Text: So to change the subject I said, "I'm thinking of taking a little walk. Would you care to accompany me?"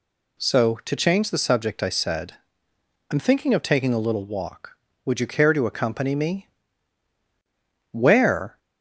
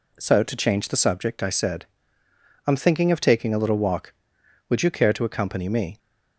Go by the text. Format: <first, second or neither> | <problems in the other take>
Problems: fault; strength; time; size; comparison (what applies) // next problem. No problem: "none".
second | goes on to say "Where"; noticeable; from 7.9 s on; 0.68 s long